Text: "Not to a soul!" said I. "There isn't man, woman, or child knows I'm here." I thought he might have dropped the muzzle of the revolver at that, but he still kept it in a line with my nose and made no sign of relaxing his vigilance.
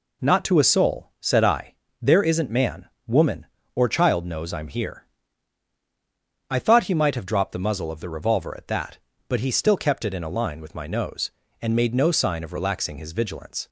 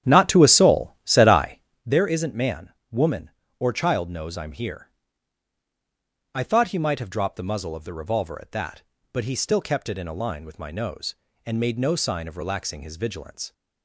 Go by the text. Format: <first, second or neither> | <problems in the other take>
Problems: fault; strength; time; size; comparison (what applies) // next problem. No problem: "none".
first | starts louder than the rest; strong; until 1.9 s; 10 dB